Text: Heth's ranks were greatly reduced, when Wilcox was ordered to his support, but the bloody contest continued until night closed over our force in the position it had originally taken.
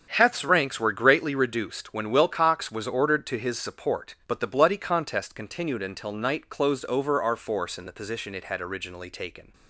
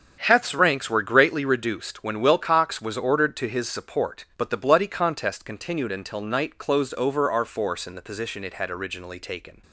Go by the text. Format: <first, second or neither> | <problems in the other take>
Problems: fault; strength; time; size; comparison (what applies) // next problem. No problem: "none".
neither | starts louder than the rest; strong; the same in both